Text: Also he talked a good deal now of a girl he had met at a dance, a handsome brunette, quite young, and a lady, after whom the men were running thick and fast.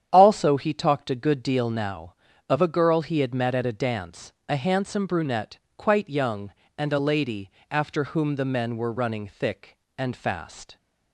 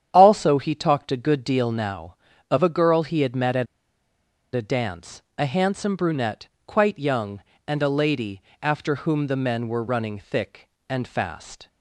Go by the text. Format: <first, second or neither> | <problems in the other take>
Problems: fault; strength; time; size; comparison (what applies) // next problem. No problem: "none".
first | starts louder than the rest; strong; until 1.1 s; 9 dB; strong in the first // pauses between "at" and "a"; noticeable; at 3.6 s; 0.89 s long